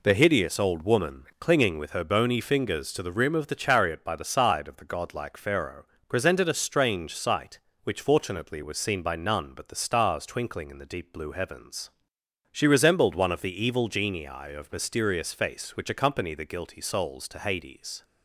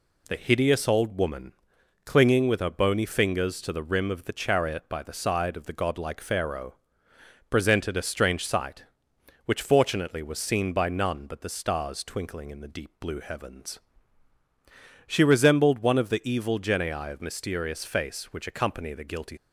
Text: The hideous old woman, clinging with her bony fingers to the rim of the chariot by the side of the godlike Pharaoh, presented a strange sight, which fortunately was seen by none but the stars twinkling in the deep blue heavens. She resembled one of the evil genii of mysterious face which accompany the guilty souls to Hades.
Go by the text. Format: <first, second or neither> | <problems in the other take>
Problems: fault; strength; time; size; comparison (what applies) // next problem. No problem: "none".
first | stops before "souls to Hades"; at 19.3 s